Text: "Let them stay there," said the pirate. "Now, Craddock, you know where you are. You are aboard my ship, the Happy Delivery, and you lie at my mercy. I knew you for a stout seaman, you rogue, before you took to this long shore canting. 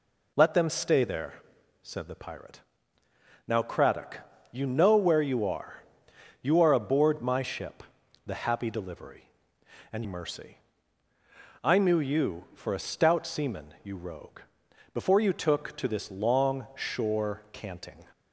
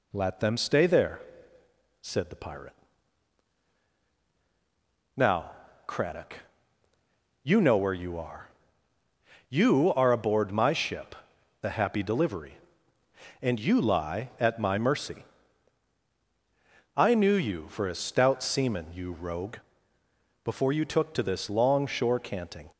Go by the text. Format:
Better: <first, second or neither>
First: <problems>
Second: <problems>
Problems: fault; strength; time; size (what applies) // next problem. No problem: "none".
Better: second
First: skips "you lie at my"; at 10.0 s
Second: none